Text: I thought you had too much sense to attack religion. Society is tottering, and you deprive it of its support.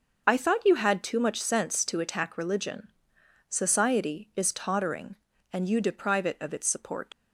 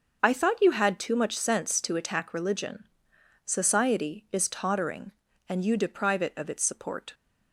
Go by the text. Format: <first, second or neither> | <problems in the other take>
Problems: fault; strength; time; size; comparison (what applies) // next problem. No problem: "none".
second | starts louder than the rest; noticeable; until 1.2 s; 6 dB; noticeable in the second // leaves "support" unfinished; at 7.1 s; 55 ms